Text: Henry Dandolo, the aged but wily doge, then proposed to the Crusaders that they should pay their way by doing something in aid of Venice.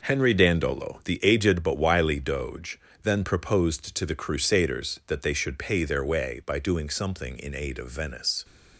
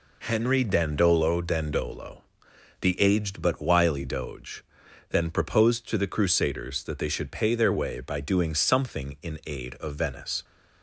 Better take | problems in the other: first | says "Dandolo" twice; at 1.4 s

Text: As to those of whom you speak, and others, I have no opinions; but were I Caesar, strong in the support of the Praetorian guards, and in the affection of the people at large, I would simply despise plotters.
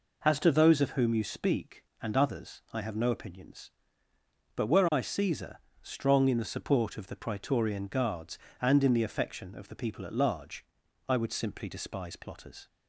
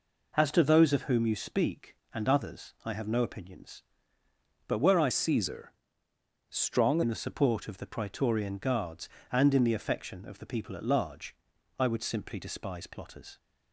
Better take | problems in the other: first | changes voice from "Caesar" to "strong"; from 5.1 to 7.0 s; 1.9 s long

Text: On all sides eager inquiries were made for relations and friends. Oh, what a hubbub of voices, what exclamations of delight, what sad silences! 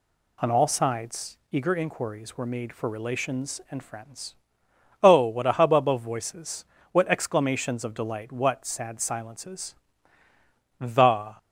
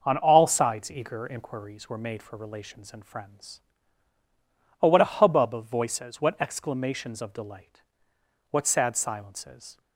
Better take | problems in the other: second | goes on to say "The"; from 10.7 s on; 0.58 s long

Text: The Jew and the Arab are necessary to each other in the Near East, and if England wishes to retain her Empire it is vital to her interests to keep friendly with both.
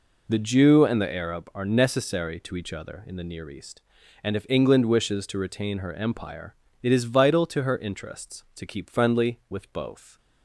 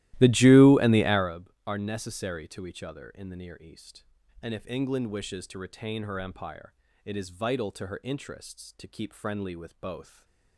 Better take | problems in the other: first | starts louder than the rest; strong; until 1.3 s; 16 dB // pauses between "Empire" and "it"; slight; at 6.7 s; 0.32 s long; slight in the first // stays silent after the last word; slight; from 10.0 s on; 0.5 s long

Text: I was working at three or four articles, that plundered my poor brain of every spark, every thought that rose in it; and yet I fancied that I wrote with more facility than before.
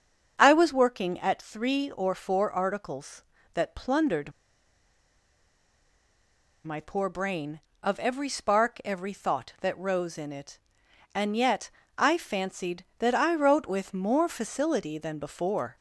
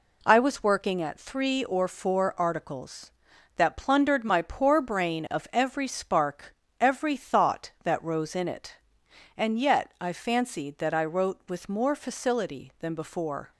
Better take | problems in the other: second | starts louder than the rest; until 1.4 s; 7 dB // pauses between "plundered" and "my"; strong; at 4.3 s; 2.3 s long // pauses between "yet" and "I"; slight; at 11.6 s; 0.26 s long

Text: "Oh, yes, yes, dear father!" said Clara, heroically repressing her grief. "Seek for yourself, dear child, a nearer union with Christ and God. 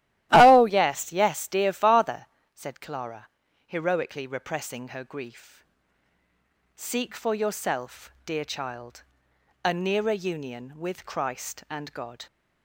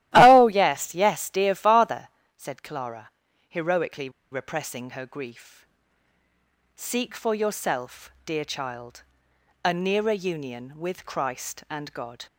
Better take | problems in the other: first | starts louder than the rest; strong; until 1.1 s; 15 dB; strong in the first // pauses between "heroically" and "repressing"; slight; at 4.1 s; 0.21 s long

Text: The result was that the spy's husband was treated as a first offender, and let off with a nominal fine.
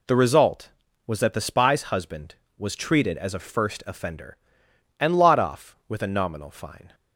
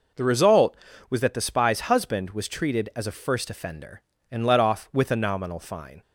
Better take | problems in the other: second | says "lot" for "let"; at 5.1 s

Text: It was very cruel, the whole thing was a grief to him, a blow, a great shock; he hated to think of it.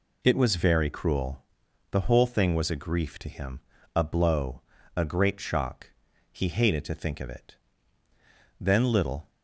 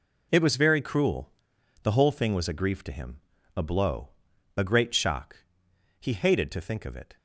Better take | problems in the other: second | goes on to say "Then little"; noticeable; from 8.5 s on; 0.70 s long

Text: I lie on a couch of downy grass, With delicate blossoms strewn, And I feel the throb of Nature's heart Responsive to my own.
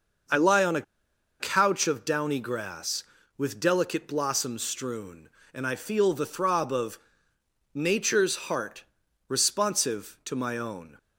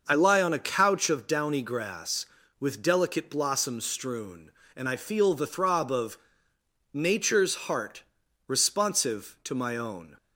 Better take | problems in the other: second | starts louder than the rest; noticeable; until 1.8 s; 6 dB; noticeable in the second // pauses between "a" and "couch"; noticeable; at 0.8 s; 0.57 s long // pauses between "of" and "Nature's"; noticeable; at 6.9 s; 0.78 s long; noticeable in the second // pauses between "heart" and "Responsive"; at 8.8 s; 0.44 s long; also in the second

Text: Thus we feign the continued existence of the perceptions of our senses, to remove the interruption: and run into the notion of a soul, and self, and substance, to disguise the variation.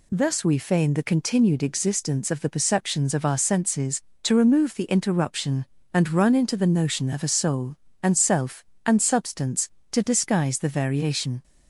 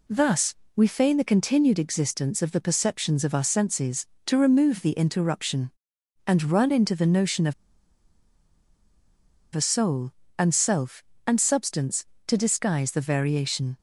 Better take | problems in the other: first | pauses between "Thus" and "we"; slight; at 0.5 s; 0.22 s long // pauses between "of" and "a"; strong; at 7.5 s; 2.0 s long

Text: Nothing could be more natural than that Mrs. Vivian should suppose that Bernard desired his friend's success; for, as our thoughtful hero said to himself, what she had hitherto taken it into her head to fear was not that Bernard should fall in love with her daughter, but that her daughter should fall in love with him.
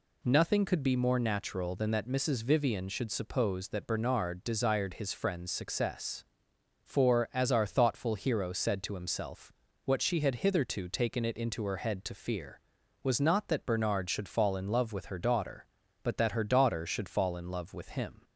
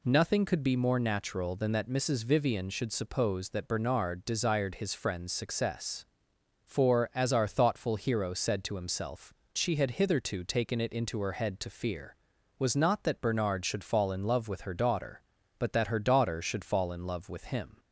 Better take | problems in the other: first | skips "what"; at 9.4 s

